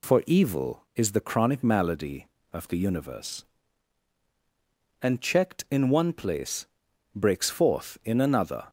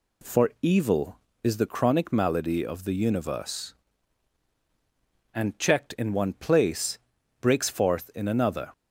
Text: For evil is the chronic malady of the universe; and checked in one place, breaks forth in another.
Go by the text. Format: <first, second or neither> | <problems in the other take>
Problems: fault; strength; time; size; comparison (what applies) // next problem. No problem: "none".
neither | none